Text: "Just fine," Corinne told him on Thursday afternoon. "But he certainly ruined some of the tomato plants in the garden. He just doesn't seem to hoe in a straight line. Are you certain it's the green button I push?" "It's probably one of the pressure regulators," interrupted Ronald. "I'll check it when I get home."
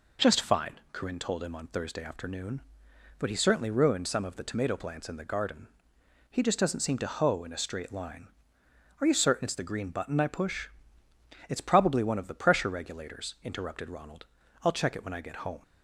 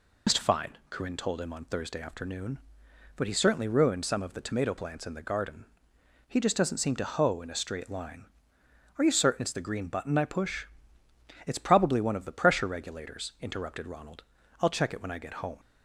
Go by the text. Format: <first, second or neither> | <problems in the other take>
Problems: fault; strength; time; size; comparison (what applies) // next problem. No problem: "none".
first | loses the start of "Just"; at 0.2 s; 100 ms